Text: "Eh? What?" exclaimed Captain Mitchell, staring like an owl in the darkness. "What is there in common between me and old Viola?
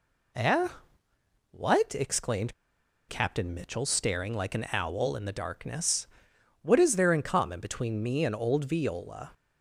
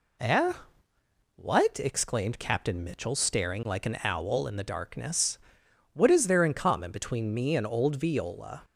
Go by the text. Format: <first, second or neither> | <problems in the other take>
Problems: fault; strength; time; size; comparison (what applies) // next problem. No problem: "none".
second | pauses between "exclaimed" and "Captain"; noticeable; at 2.5 s; 0.55 s long